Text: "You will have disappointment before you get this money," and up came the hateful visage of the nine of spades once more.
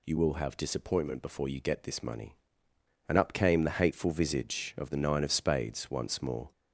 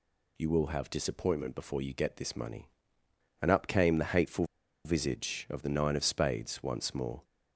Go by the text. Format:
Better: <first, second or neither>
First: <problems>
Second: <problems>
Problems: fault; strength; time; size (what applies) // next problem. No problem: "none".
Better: first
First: none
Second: pauses between "hateful" and "visage"; at 4.4 s; 0.39 s long